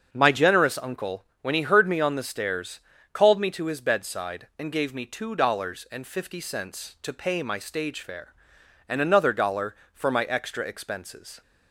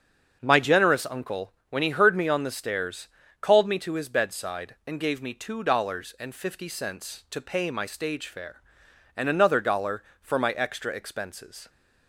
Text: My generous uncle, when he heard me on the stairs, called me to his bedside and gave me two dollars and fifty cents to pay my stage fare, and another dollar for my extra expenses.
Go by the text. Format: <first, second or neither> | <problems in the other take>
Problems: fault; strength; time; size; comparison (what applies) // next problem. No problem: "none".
neither | starts louder than the rest; the same in both